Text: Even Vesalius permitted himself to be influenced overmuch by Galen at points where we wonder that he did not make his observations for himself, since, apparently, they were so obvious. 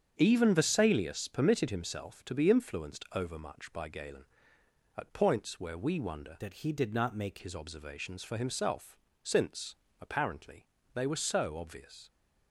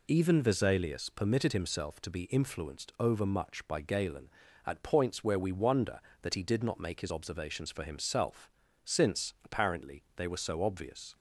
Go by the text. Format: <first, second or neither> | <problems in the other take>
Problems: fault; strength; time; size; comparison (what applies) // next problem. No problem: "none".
second | starts louder than the rest; strong; until 1.1 s; 8 dB // changes voice from "that" to "make"; from 6.4 to 7.3 s; 0.9 s long